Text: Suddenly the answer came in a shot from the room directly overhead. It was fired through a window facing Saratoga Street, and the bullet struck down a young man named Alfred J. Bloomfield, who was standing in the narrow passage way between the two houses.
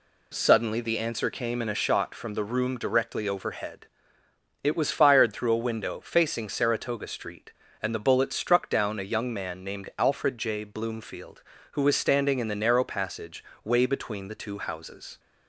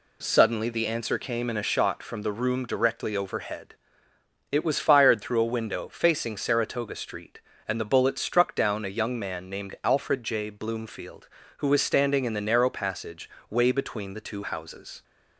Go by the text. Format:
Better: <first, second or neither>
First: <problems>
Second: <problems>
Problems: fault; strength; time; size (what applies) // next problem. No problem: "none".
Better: neither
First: pauses between "passage" and "way"; slight; at 13.4 s; 0.18 s long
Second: pauses between "passage" and "way"; slight; at 13.3 s; 0.18 s long